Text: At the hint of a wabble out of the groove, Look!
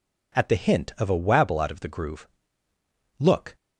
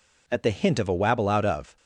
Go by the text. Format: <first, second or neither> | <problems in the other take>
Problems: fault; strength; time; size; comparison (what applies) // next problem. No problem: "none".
first | stops before "the groove Look"; at 1.7 s